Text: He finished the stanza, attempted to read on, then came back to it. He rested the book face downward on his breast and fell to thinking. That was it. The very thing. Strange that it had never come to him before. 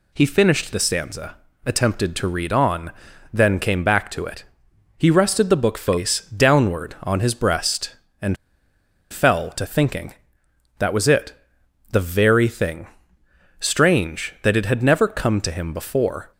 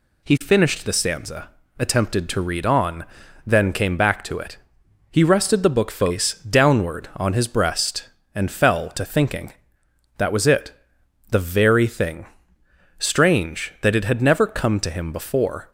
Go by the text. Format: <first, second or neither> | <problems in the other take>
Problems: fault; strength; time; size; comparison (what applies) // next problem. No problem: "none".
second | pauses between "and" and "fell"; noticeable; at 8.3 s; 0.75 s long